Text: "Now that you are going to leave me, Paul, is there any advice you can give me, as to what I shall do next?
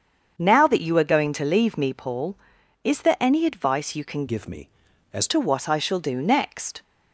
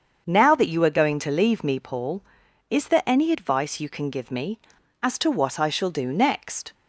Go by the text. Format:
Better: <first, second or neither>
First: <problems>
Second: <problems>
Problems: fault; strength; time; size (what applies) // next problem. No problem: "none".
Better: second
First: starts louder than the rest; strong; until 1.3 s; 7 dB // changes voice from "give" to "as"; from 4.2 to 5.2 s; 1.0 s long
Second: starts louder than the rest; until 1.2 s; 7 dB